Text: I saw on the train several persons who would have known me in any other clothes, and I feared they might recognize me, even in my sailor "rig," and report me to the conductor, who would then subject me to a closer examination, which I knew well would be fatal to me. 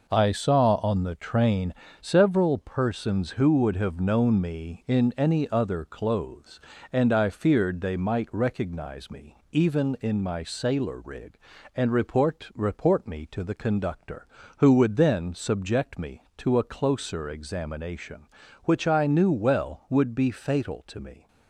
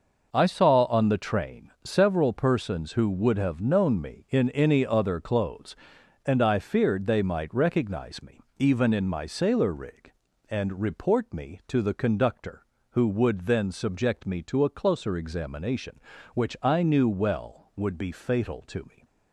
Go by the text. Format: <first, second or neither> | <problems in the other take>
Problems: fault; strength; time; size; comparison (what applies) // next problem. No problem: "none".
second | pauses between "train" and "several"; slight; at 1.7 s; 0.26 s long // says "report" twice; at 12.5 s